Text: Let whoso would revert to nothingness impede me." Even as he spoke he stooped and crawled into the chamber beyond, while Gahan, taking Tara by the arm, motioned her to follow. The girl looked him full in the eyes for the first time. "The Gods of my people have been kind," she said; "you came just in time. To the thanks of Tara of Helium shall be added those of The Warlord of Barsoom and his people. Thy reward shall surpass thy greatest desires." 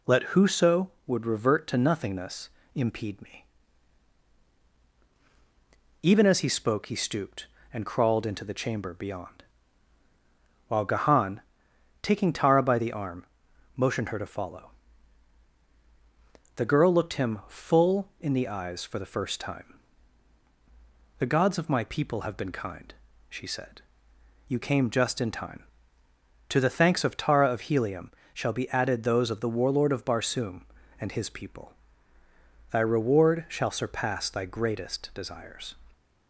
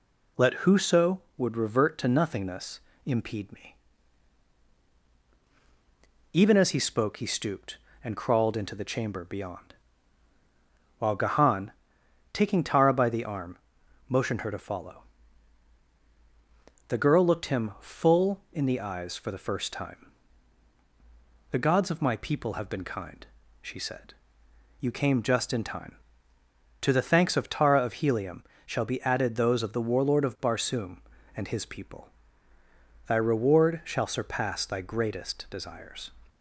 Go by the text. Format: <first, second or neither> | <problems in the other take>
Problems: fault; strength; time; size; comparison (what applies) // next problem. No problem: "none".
neither | pauses between "nothingness" and "impede"; slight; the same in both // pauses between "Helium" and "shall"; slight; the same in both